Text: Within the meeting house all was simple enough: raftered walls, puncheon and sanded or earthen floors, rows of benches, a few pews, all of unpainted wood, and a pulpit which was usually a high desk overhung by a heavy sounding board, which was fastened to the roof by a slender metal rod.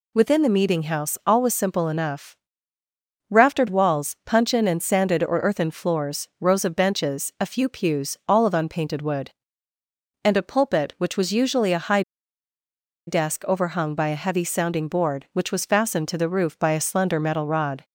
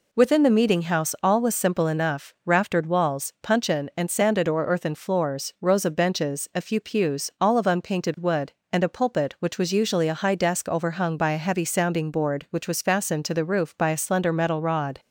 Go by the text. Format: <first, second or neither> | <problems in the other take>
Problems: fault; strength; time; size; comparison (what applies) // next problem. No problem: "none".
second | pauses between "high" and "desk"; at 12.0 s; 1.0 s long